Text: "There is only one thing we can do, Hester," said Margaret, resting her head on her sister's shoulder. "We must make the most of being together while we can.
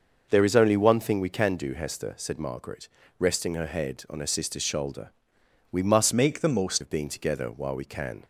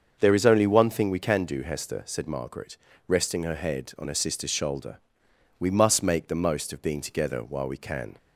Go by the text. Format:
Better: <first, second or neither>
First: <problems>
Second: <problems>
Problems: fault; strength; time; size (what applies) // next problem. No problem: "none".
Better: second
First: starts louder than the rest; noticeable; until 1.3 s; 6 dB // changes voice from "make" to "most"; from 6.1 to 6.8 s; 0.7 s long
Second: starts louder than the rest; until 1.2 s; 6.5 dB